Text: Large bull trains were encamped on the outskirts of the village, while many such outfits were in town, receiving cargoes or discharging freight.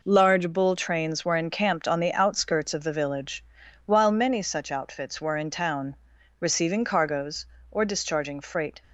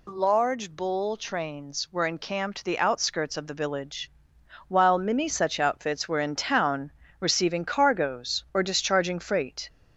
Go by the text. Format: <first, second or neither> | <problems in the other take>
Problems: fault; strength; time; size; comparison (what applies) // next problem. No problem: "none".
first | skips "on"; at 2.6 s